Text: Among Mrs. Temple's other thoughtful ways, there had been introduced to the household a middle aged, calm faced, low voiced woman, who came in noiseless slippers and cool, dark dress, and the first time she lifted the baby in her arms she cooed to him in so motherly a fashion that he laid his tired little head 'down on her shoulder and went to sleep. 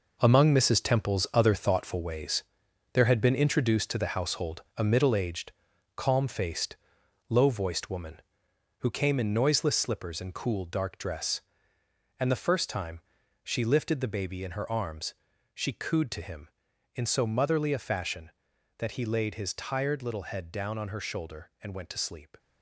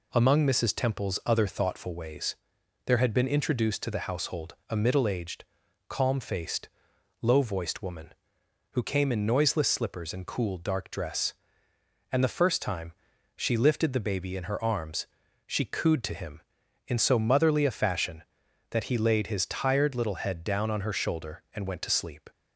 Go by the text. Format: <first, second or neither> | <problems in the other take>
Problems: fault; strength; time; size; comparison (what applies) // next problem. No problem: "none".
second | gets quieter; strong; throughout; 9 dB // pauses between "time" and "she"; at 12.9 s; 0.44 s long; also in the second // pauses between "arms" and "she"; at 15.1 s; 0.40 s long; also in the second